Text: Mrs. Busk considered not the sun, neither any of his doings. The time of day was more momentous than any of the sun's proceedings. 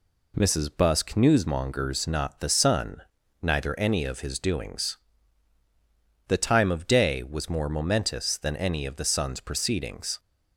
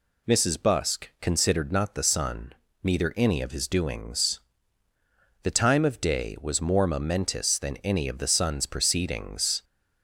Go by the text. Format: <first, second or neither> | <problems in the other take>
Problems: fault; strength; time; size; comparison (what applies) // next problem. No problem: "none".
second | says "newsmongers" for "considered"; at 1.1 s